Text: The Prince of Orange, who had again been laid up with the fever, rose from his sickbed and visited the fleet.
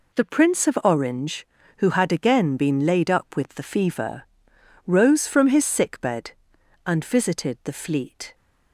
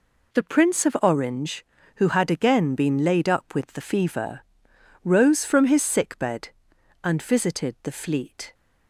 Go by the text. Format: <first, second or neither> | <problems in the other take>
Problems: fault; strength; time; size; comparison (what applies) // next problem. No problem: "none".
neither | none